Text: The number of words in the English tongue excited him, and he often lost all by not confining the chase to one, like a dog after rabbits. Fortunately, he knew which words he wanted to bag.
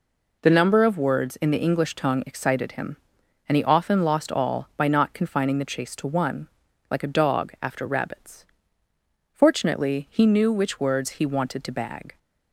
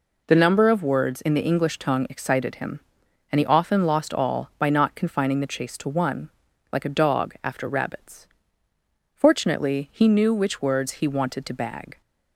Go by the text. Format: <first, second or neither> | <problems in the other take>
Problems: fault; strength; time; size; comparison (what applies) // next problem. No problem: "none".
neither | none